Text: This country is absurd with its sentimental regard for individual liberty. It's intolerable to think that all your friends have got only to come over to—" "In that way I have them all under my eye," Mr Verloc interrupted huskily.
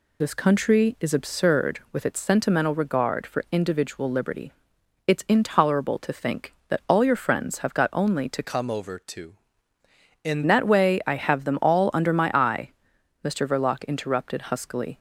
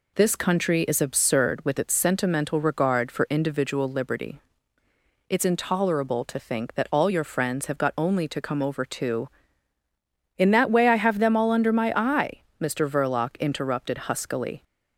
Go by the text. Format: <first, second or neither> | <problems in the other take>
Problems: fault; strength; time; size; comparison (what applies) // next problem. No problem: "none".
second | changes voice from "come" to "In"; from 8.4 to 10.4 s; 2.0 s long